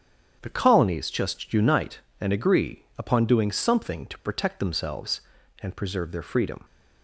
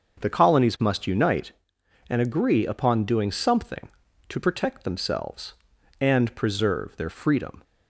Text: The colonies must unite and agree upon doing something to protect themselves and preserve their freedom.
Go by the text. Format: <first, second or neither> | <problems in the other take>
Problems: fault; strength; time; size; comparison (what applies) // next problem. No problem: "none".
second | starts louder than the rest; strong; until 1.4 s; 8.5 dB; also in the second // says "just" for "must"; at 1.0 s